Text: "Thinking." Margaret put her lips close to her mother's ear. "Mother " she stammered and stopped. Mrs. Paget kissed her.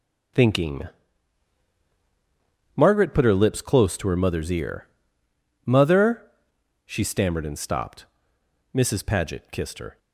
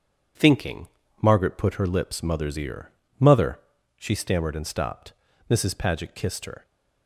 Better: first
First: starts louder than the rest; until 3.2 s; 7 dB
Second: starts louder than the rest; strong; until 1.7 s; 7.5 dB // skips "close to her"; at 2.2 s

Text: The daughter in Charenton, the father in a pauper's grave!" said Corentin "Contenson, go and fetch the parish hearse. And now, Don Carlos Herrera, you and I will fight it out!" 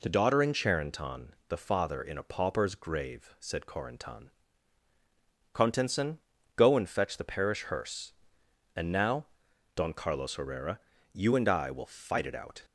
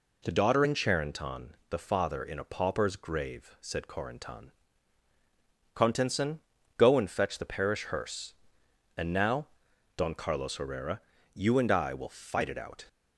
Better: neither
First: pauses between "Corentin" and "Contenson"; at 4.3 s; 1.2 s long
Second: pauses between "Corentin" and "Contenson"; at 4.5 s; 1.2 s long

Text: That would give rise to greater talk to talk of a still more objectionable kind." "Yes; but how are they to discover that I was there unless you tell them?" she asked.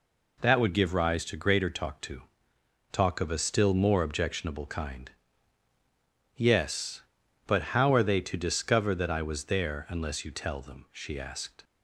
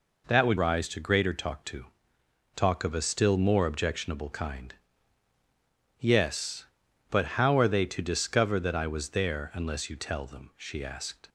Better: first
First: pauses between "to" and "talk"; noticeable; at 2.2 s; 0.68 s long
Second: skips "give"; at 0.5 s // pauses between "to" and "talk"; noticeable; at 1.8 s; 0.68 s long

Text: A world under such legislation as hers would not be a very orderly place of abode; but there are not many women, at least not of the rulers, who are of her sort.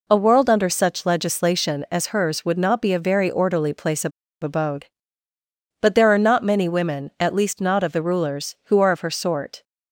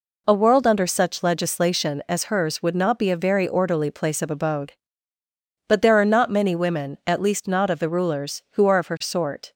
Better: second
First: pauses between "of" and "abode"; slight; at 4.1 s; 0.32 s long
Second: none

